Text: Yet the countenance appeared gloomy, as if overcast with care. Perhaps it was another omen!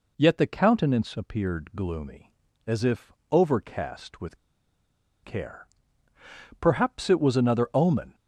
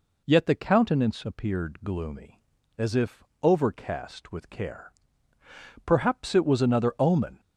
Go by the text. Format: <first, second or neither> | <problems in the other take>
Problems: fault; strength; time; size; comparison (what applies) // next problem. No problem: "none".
second | pauses between "if" and "overcast"; slight; at 3.1 s; 0.18 s long; slight in the second // pauses between "with" and "care"; noticeable; at 4.3 s; 0.87 s long